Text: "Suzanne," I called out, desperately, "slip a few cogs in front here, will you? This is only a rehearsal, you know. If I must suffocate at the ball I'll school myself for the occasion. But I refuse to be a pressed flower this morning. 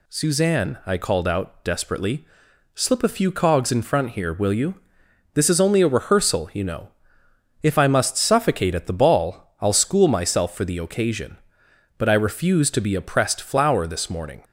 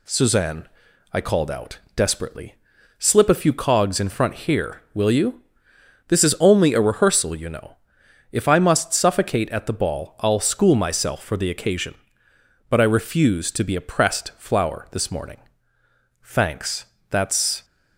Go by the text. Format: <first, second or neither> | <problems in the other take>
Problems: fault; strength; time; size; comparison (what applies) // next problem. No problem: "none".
first | goes on to say "Thanks that's"; from 16.2 s on; 1.4 s long